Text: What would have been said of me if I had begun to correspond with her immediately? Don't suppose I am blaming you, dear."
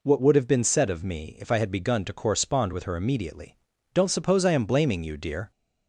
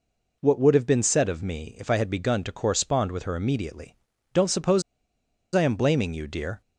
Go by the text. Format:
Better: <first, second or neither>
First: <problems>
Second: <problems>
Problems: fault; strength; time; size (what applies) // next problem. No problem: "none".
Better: first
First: none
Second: pauses between "suppose" and "I"; noticeable; at 4.8 s; 0.72 s long